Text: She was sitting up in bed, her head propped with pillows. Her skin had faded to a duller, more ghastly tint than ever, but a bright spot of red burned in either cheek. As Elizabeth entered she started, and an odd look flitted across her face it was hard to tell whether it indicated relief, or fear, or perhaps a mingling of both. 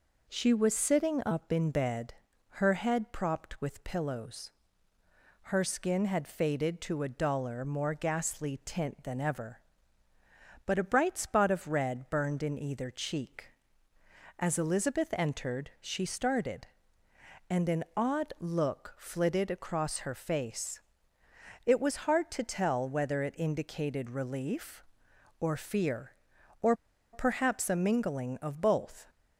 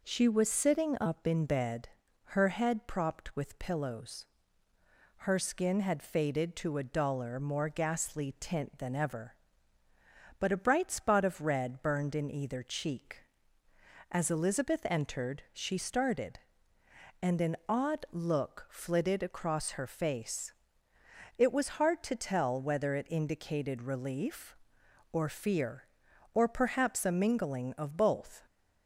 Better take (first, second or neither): second